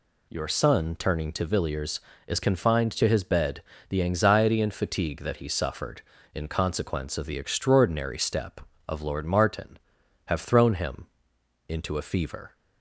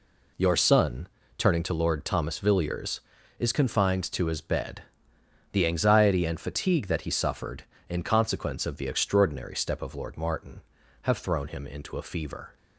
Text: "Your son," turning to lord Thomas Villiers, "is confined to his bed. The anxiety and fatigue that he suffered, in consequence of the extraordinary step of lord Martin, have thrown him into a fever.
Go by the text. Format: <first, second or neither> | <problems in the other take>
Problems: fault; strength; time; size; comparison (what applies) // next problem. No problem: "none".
second | skips "lord Thomas"; at 1.4 s // pauses between "him" and "into"; noticeable; at 11.0 s; 0.62 s long